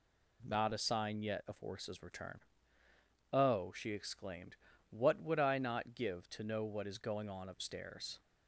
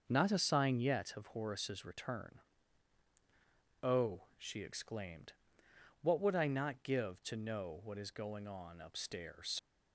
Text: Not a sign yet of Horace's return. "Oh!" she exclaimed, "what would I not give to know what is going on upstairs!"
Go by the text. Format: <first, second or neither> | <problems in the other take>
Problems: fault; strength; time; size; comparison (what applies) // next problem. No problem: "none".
first | starts louder than the rest; until 1.0 s; 6.5 dB // leaves "upstairs" unfinished; at 9.5 s; 60 ms